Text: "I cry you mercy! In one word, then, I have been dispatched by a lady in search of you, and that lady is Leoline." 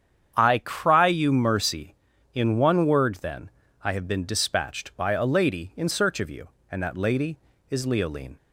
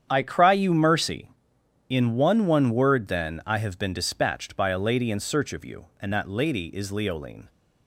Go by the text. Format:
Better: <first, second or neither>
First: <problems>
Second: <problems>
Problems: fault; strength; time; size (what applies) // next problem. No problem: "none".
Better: first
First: starts louder than the rest; strong; until 1.3 s; 8 dB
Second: starts louder than the rest; strong; until 1.1 s; 8.5 dB // says "one" twice; at 2.4 s